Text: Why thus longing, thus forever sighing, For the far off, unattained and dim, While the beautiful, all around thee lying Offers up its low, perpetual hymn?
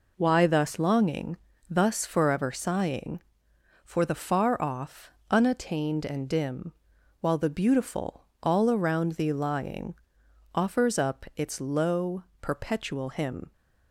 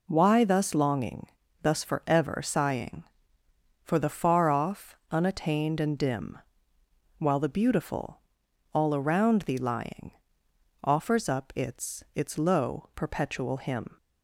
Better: first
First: pauses between "lying" and "Offers"; noticeable; at 9.9 s; 0.60 s long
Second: pauses between "lying" and "Offers"; noticeable; at 10.1 s; 0.72 s long // says "its" twice; at 12.1 s

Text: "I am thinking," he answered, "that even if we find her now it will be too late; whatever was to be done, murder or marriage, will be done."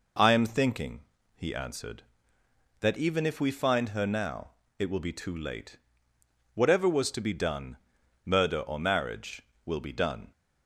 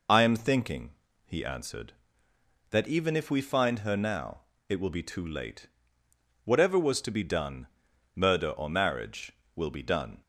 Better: first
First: pauses between "now" and "it"; slight; at 4.4 s; 0.30 s long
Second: loses the start of "I"; at 0.0 s; 35 ms // pauses between "now" and "it"; slight; at 4.3 s; 0.30 s long

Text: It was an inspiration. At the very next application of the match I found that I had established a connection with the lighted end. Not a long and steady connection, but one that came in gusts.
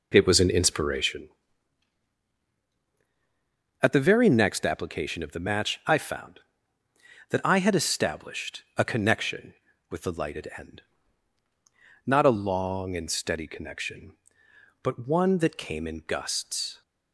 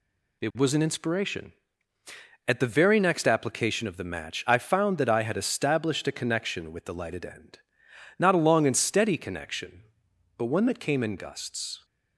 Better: second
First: starts louder than the rest; until 1.3 s; 4 dB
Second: none

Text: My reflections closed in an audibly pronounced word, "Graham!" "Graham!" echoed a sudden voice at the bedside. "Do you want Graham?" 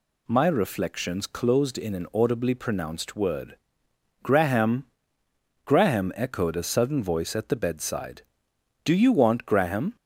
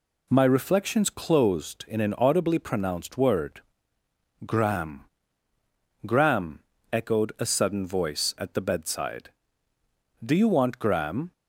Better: neither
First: none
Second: none

